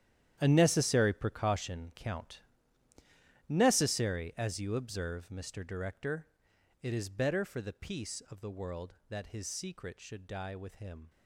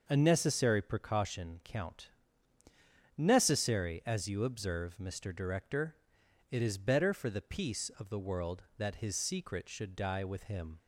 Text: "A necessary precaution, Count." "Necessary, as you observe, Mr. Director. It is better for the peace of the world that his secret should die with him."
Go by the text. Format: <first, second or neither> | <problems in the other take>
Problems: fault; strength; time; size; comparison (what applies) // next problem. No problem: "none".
second | gets quieter; strong; throughout; 15 dB // starts louder than the rest; strong; until 1.4 s; 10.5 dB; noticeable in the second